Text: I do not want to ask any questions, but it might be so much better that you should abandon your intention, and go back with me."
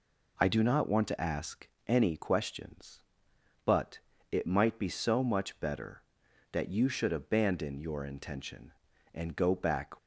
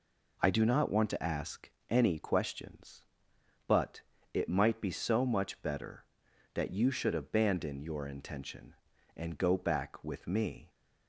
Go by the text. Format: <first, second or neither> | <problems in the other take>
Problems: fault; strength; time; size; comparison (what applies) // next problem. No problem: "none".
second | pauses between "ask" and "any"; slight; at 1.6 s; 0.18 s long; slight in the second // pauses between "but" and "it"; slight; at 3.9 s; 0.34 s long; slight in the second // stops before "with me"; at 9.9 s